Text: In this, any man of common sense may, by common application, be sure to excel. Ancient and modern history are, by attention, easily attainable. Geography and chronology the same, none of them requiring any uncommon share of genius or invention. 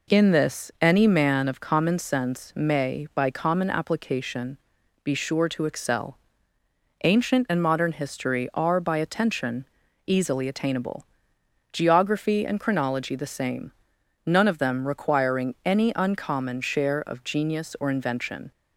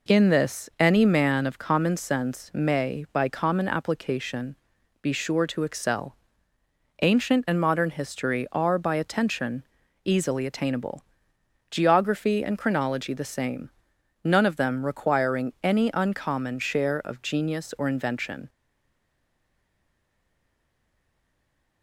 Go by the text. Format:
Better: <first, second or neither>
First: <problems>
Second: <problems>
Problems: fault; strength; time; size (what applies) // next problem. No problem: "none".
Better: first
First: none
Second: stays silent after the last word; strong; from 18.4 s on; 3.4 s long